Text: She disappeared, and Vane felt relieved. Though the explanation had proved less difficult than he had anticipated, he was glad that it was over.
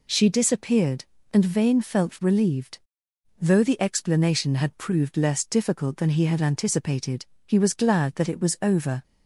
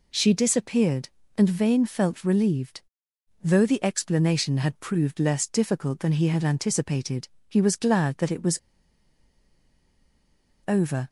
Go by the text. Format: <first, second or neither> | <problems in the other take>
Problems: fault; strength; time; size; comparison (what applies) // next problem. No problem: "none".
first | pauses between "was" and "over"; strong; at 8.5 s; 2.0 s long